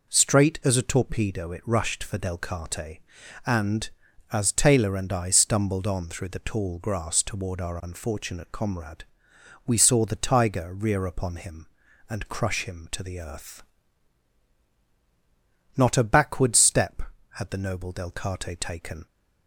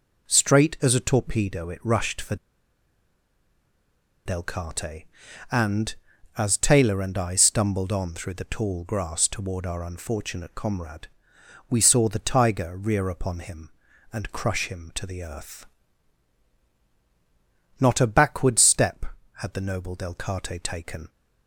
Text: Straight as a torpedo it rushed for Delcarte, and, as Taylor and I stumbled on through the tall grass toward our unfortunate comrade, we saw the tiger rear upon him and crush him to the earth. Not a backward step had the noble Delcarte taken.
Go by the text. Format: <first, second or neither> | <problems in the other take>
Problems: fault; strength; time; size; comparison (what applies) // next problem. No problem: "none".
first | pauses between "for" and "Delcarte"; strong; at 2.3 s; 1.9 s long